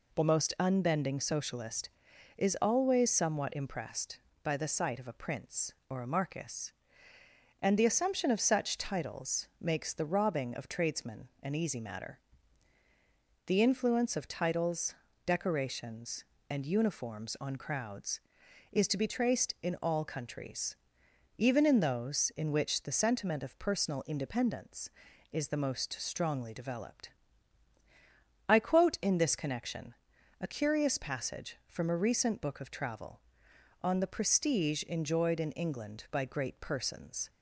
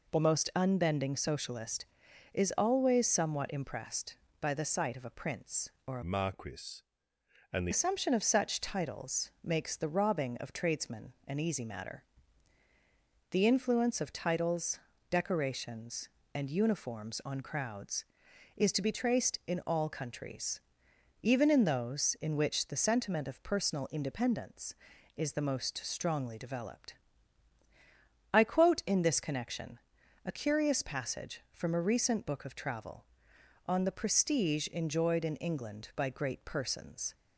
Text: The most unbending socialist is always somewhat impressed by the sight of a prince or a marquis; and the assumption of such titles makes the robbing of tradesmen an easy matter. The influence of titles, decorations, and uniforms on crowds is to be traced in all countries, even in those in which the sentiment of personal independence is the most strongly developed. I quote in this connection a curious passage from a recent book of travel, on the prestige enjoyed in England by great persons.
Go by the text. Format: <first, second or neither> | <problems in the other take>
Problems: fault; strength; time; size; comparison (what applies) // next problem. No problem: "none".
first | changes voice from "marquis" to "the"; from 6.0 to 7.7 s; 1.7 s long // pauses between "connection" and "a"; noticeable; at 29.7 s; 0.48 s long; noticeable in the first